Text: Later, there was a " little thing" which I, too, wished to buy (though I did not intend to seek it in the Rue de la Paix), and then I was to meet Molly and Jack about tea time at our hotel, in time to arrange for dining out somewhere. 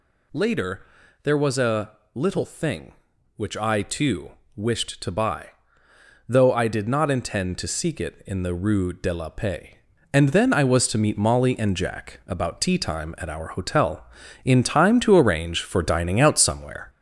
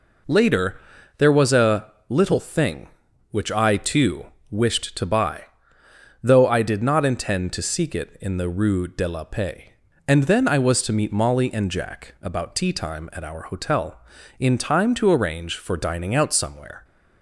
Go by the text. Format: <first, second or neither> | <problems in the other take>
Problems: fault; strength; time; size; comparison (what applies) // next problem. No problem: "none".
second | gets louder; noticeable; throughout; 5.5 dB